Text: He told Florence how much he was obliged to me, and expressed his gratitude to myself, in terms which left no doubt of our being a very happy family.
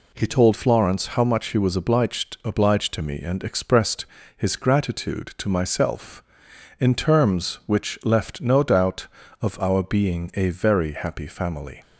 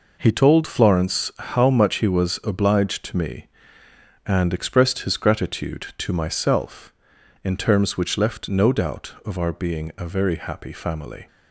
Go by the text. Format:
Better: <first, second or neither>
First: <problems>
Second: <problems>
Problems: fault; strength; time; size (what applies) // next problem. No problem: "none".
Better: second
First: says "obliged" twice; at 2.4 s // pauses between "expressed" and "his"; slight; at 4.0 s; 0.30 s long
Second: none